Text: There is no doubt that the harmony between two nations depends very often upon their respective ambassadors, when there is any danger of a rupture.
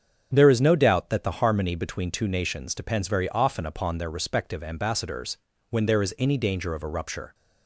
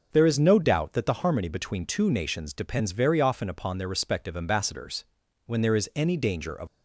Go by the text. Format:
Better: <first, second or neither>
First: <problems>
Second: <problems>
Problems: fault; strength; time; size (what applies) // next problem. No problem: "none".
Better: first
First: starts louder than the rest; strong; until 1.3 s; 7.5 dB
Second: starts louder than the rest; noticeable; until 1.1 s; 6 dB // stops before "a rupture"; at 6.6 s